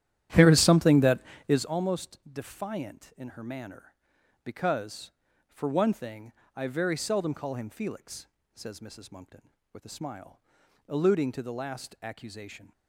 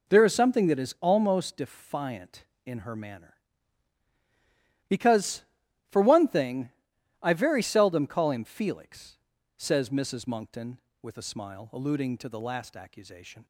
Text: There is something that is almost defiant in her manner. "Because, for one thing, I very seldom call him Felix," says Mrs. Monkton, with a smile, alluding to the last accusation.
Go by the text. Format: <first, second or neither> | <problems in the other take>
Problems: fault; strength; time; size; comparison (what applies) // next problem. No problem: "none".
second | starts louder than the rest; strong; until 1.7 s; 12 dB